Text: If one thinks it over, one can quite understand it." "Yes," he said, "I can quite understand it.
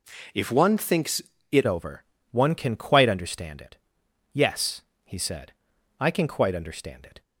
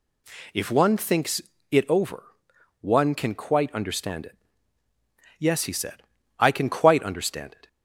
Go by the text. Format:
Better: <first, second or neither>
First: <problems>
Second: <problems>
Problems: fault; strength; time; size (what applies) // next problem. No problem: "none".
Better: second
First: pauses between "thinks" and "it"; slight; at 1.2 s; 0.30 s long // changes voice at "over"; from 1.6 s on; 5.6 s long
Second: pauses between "thinks" and "it"; slight; at 1.4 s; 0.30 s long